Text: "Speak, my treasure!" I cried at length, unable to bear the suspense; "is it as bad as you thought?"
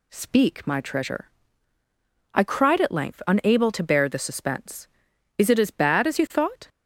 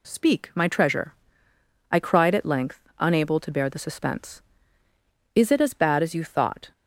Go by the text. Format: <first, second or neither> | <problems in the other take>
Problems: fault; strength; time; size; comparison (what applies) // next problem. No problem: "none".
neither | none